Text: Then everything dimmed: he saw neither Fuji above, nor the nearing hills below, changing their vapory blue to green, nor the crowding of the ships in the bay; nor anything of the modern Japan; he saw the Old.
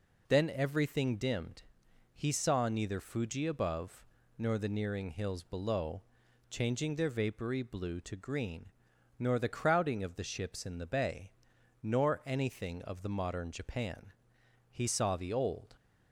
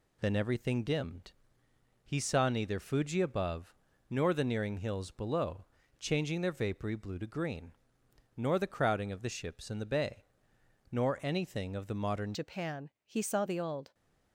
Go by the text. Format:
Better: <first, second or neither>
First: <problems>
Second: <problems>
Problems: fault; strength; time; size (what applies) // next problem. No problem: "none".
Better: first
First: none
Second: changes voice at "Japan"; from 12.3 s on; 1.6 s long